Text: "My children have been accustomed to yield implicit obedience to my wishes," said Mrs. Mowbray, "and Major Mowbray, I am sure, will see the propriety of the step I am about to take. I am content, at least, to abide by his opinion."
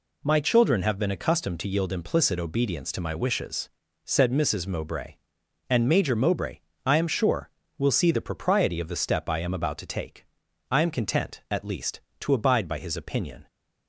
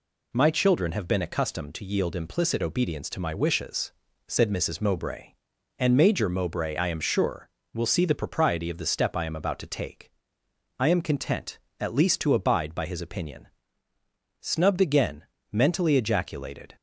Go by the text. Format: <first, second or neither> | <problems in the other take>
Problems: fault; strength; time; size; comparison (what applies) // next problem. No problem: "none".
first | goes on to say "Snubbed again mentally ejaculated"; strong; from 14.4 s on; 2.3 s long